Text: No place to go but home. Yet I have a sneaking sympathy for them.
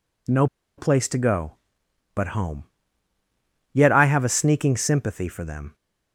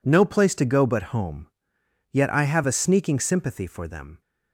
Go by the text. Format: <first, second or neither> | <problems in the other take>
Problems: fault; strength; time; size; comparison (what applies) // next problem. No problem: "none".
second | pauses between "No" and "place"; slight; at 0.4 s; 0.32 s long